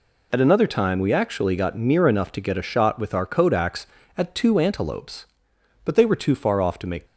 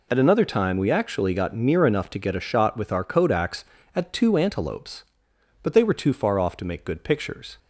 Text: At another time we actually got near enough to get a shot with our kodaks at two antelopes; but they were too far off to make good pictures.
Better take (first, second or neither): second